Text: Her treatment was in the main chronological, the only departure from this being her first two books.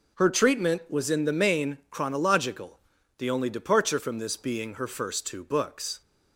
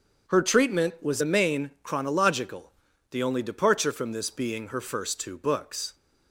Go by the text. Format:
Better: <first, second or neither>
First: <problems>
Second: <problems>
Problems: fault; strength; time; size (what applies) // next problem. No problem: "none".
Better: first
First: none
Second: starts louder than the rest; until 1.3 s; 7 dB // skips "in"; at 1.2 s